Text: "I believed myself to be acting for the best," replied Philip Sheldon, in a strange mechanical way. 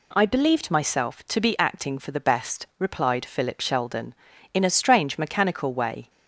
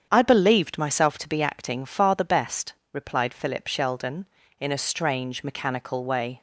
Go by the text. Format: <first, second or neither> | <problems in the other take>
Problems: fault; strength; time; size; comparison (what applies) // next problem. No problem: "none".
first | starts louder than the rest; strong; until 1.1 s; 8 dB // says "far" for "for"; at 1.8 s